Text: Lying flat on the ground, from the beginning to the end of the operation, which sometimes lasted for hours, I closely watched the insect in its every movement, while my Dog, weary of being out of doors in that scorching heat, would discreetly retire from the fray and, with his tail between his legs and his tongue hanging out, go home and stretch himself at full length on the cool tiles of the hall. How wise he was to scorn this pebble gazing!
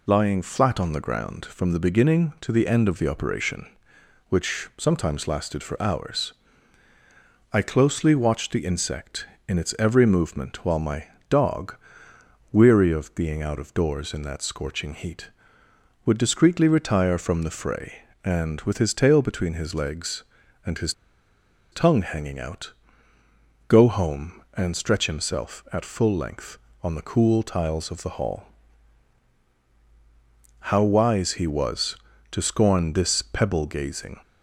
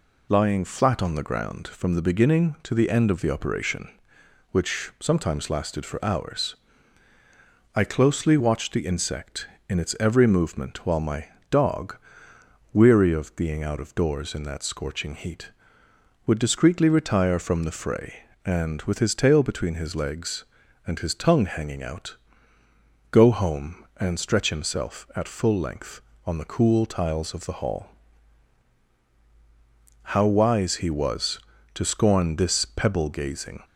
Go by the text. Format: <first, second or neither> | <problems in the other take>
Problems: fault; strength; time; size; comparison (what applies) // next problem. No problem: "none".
second | pauses between "my" and "Dog"; slight; at 11.0 s; 0.22 s long; slight in the second // pauses between "his" and "tongue"; noticeable; at 20.9 s; 0.80 s long